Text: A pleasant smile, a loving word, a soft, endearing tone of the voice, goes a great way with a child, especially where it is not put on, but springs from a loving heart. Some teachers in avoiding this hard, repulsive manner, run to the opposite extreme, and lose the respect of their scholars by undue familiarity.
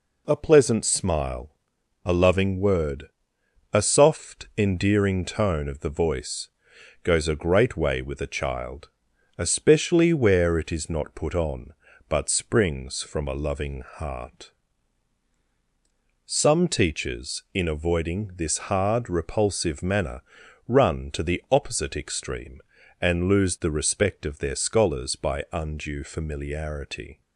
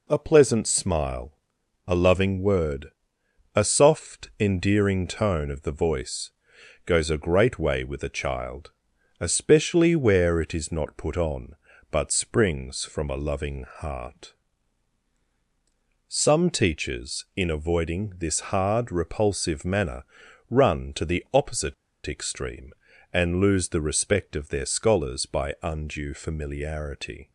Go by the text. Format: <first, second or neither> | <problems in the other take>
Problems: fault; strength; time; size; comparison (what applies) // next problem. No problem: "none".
first | pauses between "opposite" and "extreme"; slight; at 21.7 s; 0.32 s long